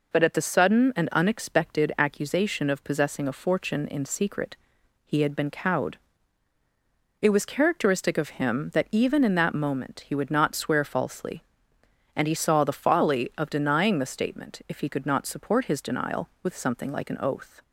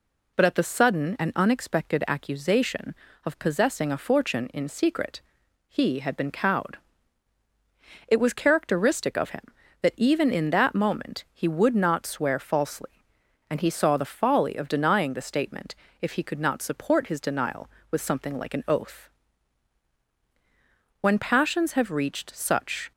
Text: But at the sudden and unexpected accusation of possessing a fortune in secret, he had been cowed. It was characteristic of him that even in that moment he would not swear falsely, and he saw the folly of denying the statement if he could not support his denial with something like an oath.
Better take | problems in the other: first | pauses between "statement" and "if"; slight; at 15.7 s; 0.24 s long // goes on to say "When passions have reached such"; strong; from 21.0 s on; 1.9 s long

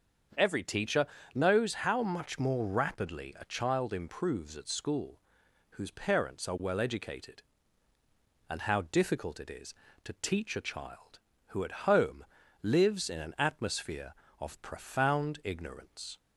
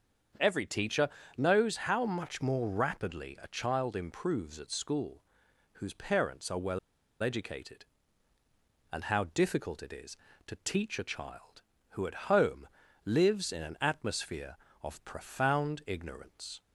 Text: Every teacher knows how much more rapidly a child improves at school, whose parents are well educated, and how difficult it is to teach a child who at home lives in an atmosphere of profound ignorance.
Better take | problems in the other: first | starts louder than the rest; strong; until 1.7 s; 7 dB; also in the first // pauses between "teacher" and "knows"; slight; at 1.0 s; 0.30 s long; slight in the first // pauses between "well" and "educated"; at 6.7 s; 0.44 s long // pauses between "home" and "lives"; at 12.6 s; 0.38 s long; also in the first

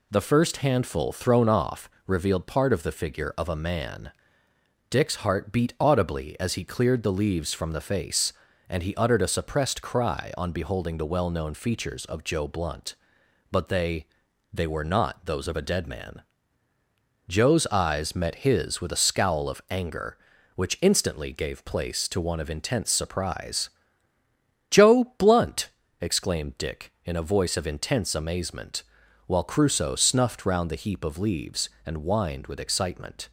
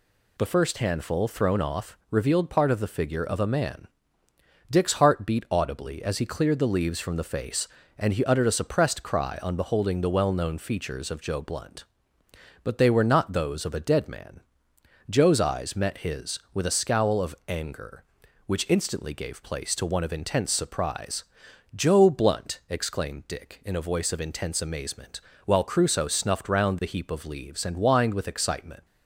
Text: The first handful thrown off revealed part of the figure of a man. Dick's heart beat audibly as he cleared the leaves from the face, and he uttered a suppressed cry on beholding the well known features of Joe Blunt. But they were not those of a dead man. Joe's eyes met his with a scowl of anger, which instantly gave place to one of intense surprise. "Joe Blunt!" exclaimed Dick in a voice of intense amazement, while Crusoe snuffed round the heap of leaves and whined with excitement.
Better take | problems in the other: second | pauses between "off" and "revealed"; slight; at 1.8 s; 0.18 s long // says "they" twice; at 14.5 s

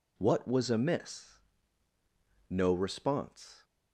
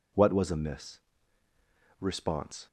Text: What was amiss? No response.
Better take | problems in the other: first | skips "No"; at 1.4 s

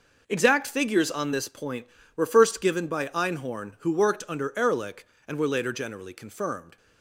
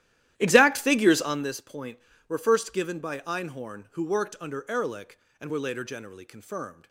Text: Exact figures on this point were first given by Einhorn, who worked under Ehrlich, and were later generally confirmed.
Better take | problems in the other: first | starts louder than the rest; strong; until 1.5 s; 13 dB

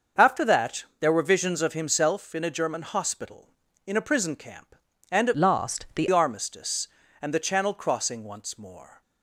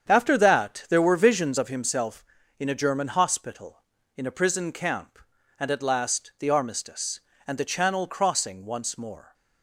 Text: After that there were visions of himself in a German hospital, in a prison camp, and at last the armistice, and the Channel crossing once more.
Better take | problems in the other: second | starts louder than the rest; until 1.3 s; 6.5 dB; strong in the second // changes voice from "last" to "the"; from 5.3 to 6.0 s; 0.7 s long

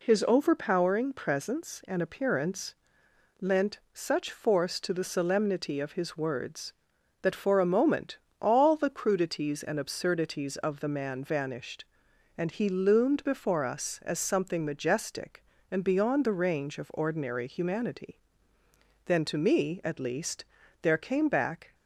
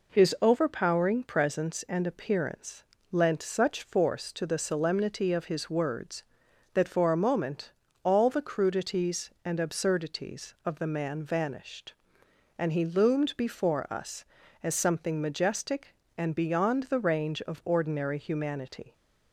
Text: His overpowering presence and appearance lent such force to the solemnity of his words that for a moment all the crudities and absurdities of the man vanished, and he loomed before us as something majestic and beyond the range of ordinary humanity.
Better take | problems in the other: second | pauses between "appearance" and "lent"; noticeable; at 2.7 s; 0.66 s long; slight in the second // pauses between "lent" and "such"; slight; at 3.7 s; 0.16 s long // pauses between "moment" and "all"; slight; at 8.1 s; 0.22 s long; slight in the second // goes on to say "Then to me at least there came back"; strong; from 19.0 s on; 2.7 s long

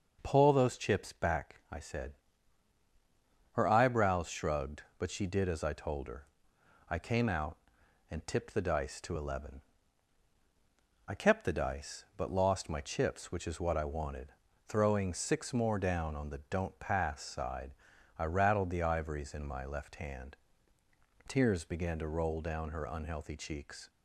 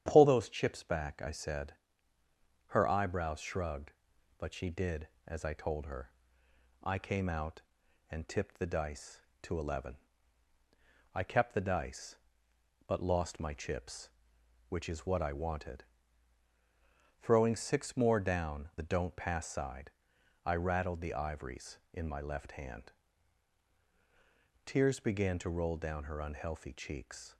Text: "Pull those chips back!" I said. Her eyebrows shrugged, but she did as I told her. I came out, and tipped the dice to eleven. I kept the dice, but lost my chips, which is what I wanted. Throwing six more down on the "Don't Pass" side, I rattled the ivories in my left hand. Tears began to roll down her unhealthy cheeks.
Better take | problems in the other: first | starts louder than the rest; strong; until 1.0 s; 10 dB // skips "on"; at 18.7 s

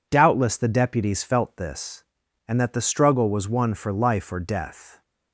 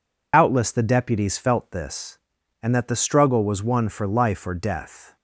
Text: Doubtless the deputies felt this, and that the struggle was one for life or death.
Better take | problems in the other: first | loses the start of "Doubtless"; at 0.3 s; 95 ms

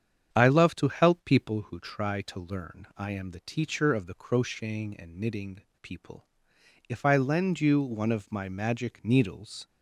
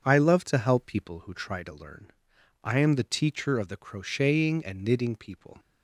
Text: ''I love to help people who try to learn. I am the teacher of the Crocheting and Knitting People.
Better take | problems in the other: second | starts louder than the rest; strong; until 1.3 s; 8 dB; also in the second // pauses between "Knitting" and "People"; slight; at 5.6 s; 0.20 s long // goes on to say "If I lend you one of my magic needles"; strong; from 6.8 s on; 2.7 s long

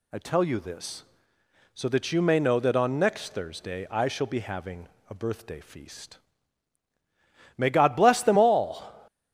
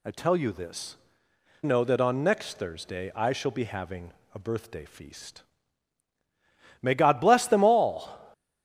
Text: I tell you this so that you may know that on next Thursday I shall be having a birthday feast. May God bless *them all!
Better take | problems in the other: first | skips "so that you may"; at 1.2 s // pauses between "having" and "a"; slight; at 4.1 s; 0.22 s long; slight in the first

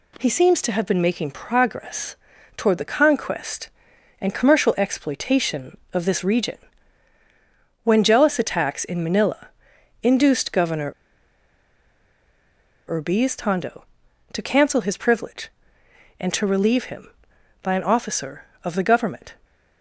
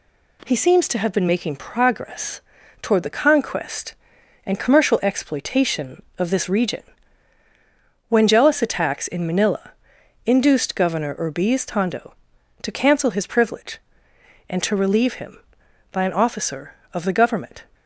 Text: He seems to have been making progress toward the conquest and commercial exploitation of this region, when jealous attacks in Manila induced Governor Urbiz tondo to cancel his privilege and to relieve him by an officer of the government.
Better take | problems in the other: second | pauses between "progress" and "toward"; at 2.1 s; 0.40 s long; also in the second // pauses between "Manila" and "induced"; noticeable; at 9.4 s; 0.54 s long; noticeable in the second // pauses between "Governor" and "Urbiz"; strong; at 10.9 s; 1.9 s long

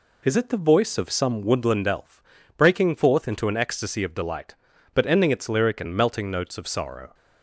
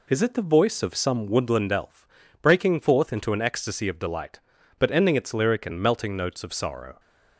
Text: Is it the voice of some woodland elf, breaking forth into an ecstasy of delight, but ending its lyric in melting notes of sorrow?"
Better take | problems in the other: neither | none

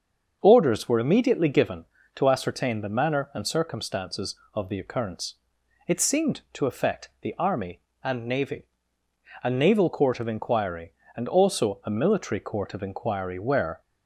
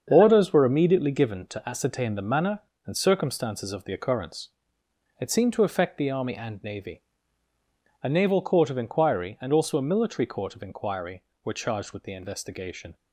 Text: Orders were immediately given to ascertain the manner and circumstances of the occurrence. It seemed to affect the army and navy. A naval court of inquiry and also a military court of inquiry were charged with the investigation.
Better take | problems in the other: second | starts louder than the rest; until 1.4 s; 6.5 dB; strong in the second // stops before "charged with the investigation"; at 13.8 s

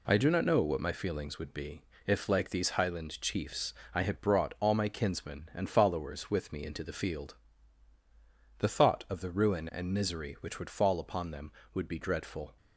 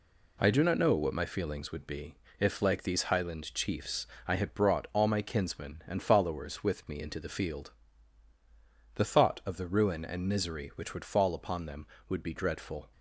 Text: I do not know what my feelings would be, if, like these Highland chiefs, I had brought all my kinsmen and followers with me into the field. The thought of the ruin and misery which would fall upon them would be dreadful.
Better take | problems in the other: neither | none

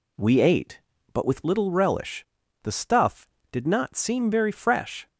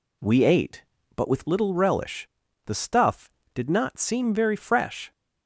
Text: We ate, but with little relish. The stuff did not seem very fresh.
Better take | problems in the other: neither | none

